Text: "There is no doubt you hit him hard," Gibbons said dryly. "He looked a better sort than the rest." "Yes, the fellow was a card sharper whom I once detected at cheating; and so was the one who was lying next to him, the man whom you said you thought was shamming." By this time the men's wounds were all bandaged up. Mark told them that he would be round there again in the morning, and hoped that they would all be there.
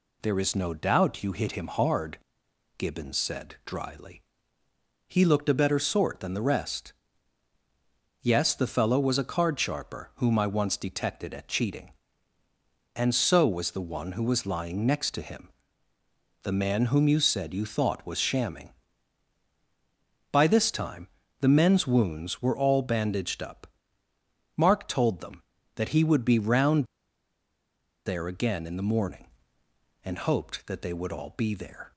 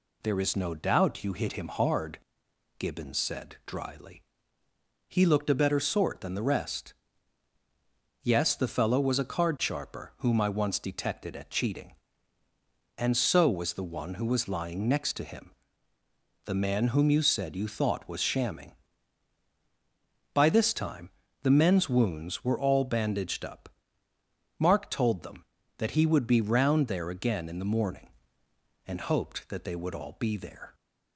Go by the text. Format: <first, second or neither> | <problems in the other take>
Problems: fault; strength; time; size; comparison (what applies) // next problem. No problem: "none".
second | pauses between "time" and "the"; slight; at 21.0 s; 0.32 s long; slight in the second // pauses between "round" and "there"; at 26.8 s; 1.2 s long